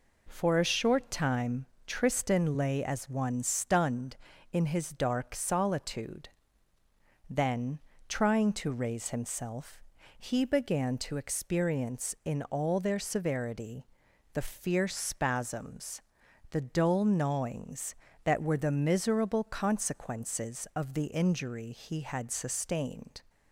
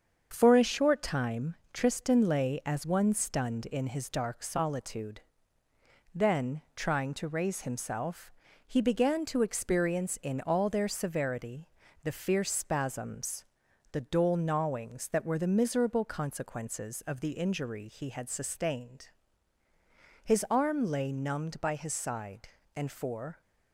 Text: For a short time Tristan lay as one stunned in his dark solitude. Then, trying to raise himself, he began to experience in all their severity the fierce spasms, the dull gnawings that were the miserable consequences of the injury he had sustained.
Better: first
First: pauses between "time" and "Tristan"; slight; at 1.6 s; 0.20 s long // pauses between "severity" and "the"; noticeable; at 13.8 s; 0.46 s long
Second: starts louder than the rest; until 1.3 s; 7 dB // pauses between "time" and "Tristan"; slight; at 1.5 s; 0.18 s long // pauses between "severity" and "the"; at 11.6 s; 0.38 s long // goes on to say "His arm lay numbed by his side and for"; strong; from 20.2 s on; 3.1 s long

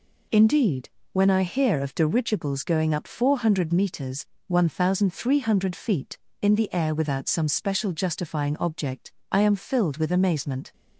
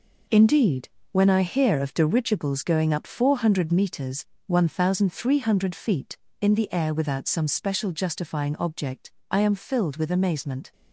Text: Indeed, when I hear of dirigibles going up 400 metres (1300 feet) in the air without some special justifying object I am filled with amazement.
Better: first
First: pauses between "object" and "I"; slight; at 9.1 s; 0.22 s long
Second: gets quieter; strong; throughout; 7.5 dB // pauses between "object" and "I"; slight; at 9.0 s; 0.22 s long

